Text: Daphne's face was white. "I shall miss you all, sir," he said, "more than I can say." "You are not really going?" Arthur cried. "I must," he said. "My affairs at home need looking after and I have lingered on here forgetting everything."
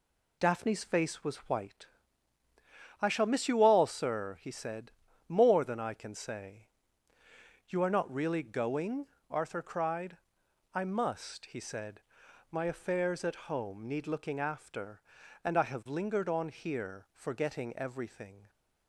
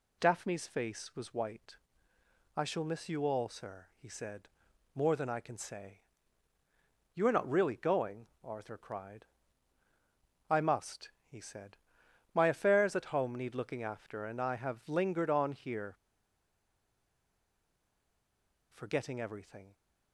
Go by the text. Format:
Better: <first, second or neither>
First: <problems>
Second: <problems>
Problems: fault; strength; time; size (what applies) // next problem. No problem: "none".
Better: first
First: none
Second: pauses between "here" and "forgetting"; strong; at 15.9 s; 2.7 s long